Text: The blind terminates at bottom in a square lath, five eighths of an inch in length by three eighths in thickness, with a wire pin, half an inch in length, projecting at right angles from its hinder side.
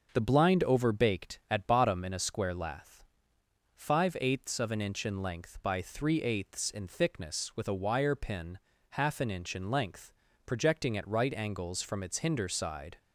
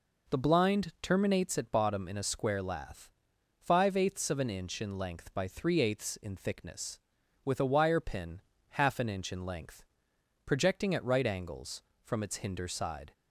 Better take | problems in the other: second | starts louder than the rest; until 1.1 s; 6.5 dB // says "overbaked" for "terminates"; at 0.6 s

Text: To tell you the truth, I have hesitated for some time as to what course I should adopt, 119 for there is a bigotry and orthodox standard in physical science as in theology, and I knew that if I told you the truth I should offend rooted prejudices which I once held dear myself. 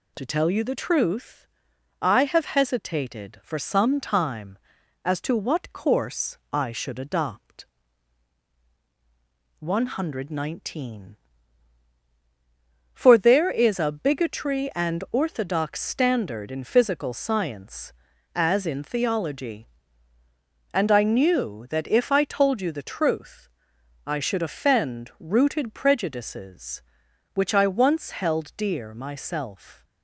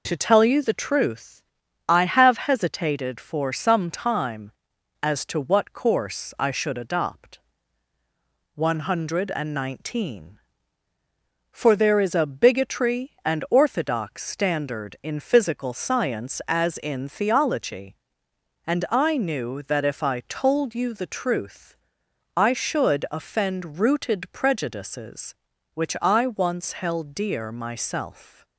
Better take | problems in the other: neither | pauses between "truth" and "I"; noticeable; the same in both

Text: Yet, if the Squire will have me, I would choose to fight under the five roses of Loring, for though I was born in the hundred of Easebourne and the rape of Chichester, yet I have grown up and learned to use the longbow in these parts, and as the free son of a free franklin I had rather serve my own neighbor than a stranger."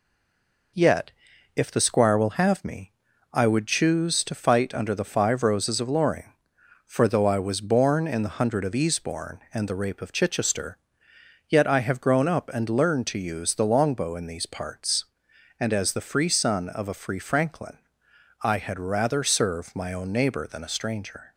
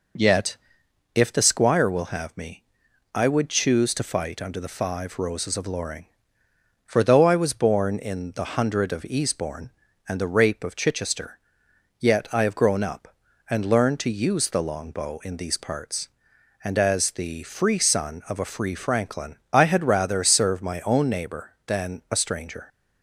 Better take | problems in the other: second | stays silent before the first word; slight; until 0.7 s; 0.7 s long // pauses between "franklin" and "I"; noticeable; at 17.7 s; 0.64 s long; slight in the second

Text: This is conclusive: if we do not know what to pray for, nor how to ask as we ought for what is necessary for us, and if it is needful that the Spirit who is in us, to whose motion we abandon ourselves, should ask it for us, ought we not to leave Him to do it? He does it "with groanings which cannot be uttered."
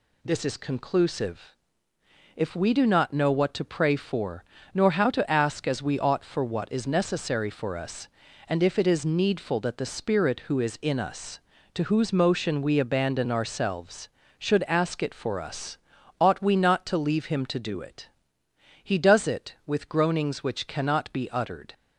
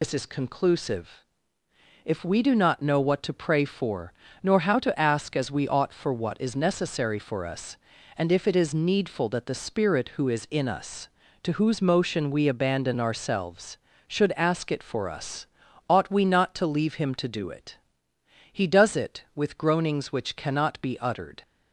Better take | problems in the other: first | loses the start of "This"; at 0.0 s; 95 ms

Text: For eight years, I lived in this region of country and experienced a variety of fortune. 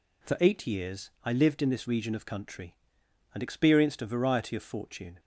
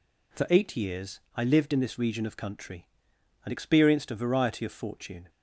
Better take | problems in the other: neither | none

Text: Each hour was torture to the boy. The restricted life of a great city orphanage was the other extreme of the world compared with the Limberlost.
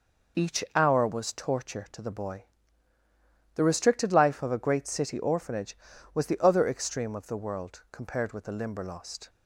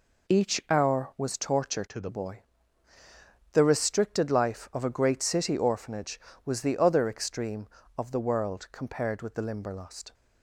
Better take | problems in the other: first | changes voice from "to" to "the"; from 1.8 to 2.0 s; 0.2 s long

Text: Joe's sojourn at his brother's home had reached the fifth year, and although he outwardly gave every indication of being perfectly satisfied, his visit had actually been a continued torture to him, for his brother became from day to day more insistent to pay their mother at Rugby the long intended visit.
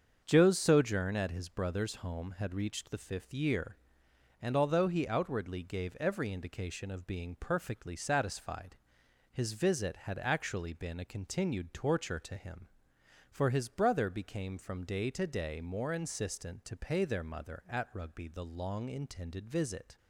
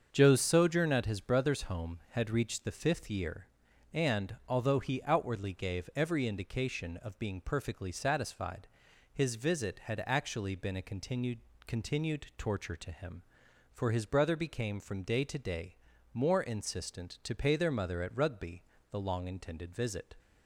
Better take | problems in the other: first | starts louder than the rest; until 1.1 s; 7 dB; also in the first // says "continued" twice; at 11.6 s // pauses between "day" and "more"; slight; at 15.7 s; 0.36 s long // pauses between "Rugby" and "the"; slight; at 18.6 s; 0.28 s long

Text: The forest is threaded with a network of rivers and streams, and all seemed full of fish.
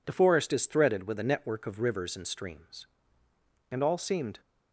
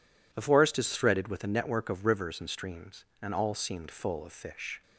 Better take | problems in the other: second | stops before "full of fish"; at 4.4 s

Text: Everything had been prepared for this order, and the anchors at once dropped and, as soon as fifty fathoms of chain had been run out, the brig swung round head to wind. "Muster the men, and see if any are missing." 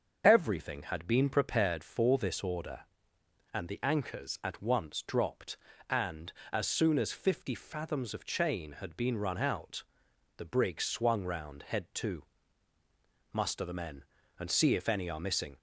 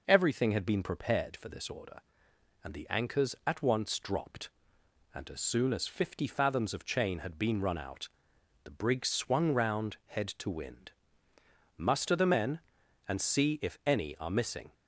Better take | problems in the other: second | starts louder than the rest; until 1.2 s; 6.5 dB // skips "wind"; at 12.7 s

